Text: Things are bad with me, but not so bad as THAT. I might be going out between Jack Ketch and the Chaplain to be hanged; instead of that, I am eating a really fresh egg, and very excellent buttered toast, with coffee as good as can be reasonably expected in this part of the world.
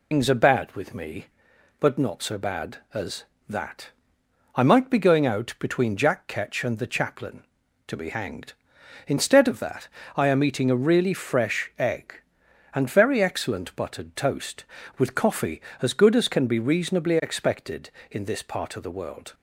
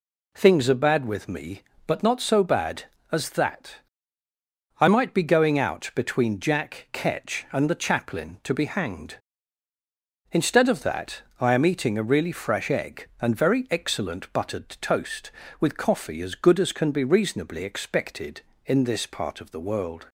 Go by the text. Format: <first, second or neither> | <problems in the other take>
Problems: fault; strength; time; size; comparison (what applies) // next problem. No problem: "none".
second | loses the start of "Things"; at 0.1 s; 135 ms